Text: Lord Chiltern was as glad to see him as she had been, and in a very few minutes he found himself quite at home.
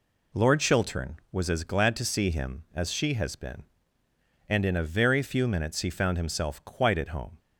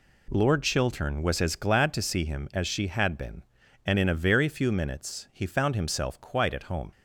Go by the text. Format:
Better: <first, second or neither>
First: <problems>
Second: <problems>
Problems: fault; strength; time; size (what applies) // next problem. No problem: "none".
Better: second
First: says "has" for "had"; at 3.1 s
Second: none